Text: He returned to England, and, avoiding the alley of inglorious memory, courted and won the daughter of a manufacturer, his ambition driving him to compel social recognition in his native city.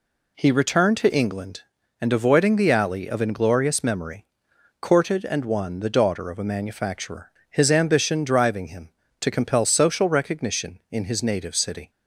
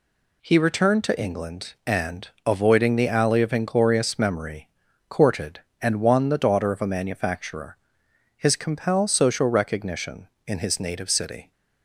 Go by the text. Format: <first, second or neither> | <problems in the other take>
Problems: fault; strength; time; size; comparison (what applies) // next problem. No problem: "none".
first | skips "ambition driving him to"; at 8.5 s